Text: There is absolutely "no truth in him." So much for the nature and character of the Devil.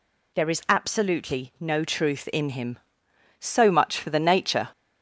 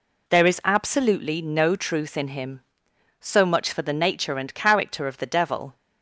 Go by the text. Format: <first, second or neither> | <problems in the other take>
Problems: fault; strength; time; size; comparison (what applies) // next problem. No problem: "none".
second | stops before "and character of the Devil"; at 4.7 s